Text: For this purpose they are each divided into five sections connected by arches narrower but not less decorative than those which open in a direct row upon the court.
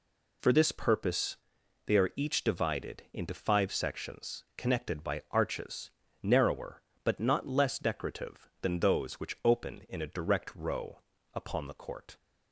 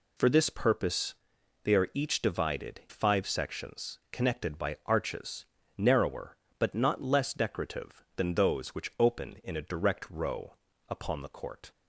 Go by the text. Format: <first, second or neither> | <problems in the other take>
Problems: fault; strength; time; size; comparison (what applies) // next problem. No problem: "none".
first | pauses between "purpose" and "they"; noticeable; at 1.1 s; 0.48 s long; noticeable in the first // skips "into"; at 2.8 s // pauses between "arches" and "narrower"; slight; at 5.4 s; 0.32 s long; slight in the first // pauses between "row" and "upon"; slight; at 10.5 s; 0.34 s long; slight in the first